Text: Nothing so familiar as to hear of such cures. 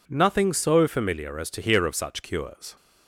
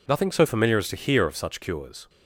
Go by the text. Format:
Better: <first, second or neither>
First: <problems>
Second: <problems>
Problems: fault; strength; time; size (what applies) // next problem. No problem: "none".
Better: neither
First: none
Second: none